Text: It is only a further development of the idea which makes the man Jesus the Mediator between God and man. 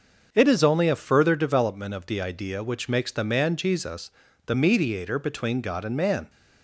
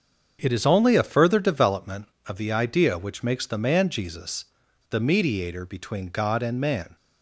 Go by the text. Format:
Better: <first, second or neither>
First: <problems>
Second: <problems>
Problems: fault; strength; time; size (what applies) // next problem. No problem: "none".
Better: neither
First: starts louder than the rest; until 1.3 s; 6.5 dB // pauses between "Jesus" and "the"; slight; at 4.1 s; 0.36 s long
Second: starts louder than the rest; until 1.4 s; 7 dB // pauses between "Jesus" and "the"; at 4.4 s; 0.43 s long